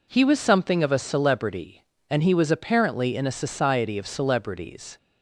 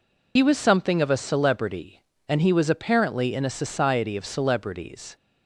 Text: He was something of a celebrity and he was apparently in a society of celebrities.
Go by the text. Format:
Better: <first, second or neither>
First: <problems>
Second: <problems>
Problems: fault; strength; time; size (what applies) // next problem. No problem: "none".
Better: first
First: none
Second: loses the start of "He"; at 0.3 s; 70 ms